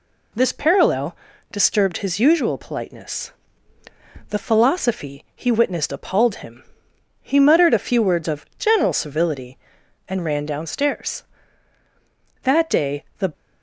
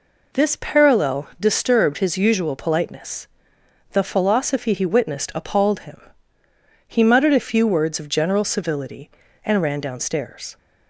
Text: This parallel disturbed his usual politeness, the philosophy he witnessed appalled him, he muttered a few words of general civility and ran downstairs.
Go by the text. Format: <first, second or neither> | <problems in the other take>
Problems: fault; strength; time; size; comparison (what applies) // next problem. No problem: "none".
second | pauses between "parallel" and "disturbed"; slight; at 1.1 s; 0.36 s long // goes on to say "That day the"; noticeable; from 12.4 s on; 0.90 s long